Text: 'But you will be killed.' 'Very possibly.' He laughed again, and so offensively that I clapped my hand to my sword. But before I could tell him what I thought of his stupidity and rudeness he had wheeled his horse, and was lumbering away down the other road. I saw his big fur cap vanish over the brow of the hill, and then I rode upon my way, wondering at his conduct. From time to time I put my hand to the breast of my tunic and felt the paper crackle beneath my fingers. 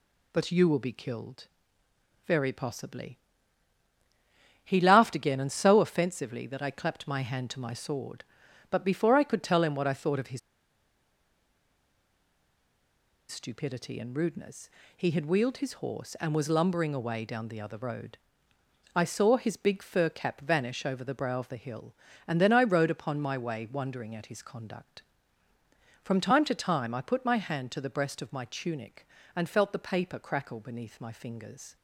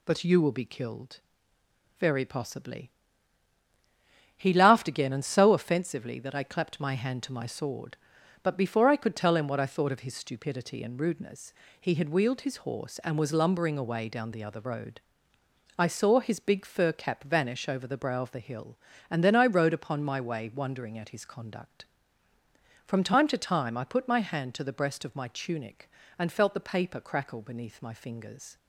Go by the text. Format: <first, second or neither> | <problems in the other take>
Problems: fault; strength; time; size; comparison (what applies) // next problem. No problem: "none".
second | pauses between "his" and "stupidity"; strong; at 10.3 s; 2.9 s long // pauses between "rudeness" and "he"; slight; at 14.6 s; 0.26 s long; slight in the second